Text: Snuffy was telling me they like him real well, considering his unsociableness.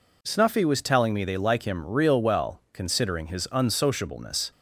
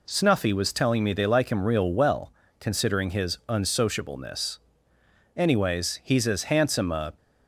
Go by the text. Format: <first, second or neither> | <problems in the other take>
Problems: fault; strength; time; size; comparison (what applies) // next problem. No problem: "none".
first | goes on to say "Anyways he's as handsome a"; strong; from 5.3 s on; 1.8 s long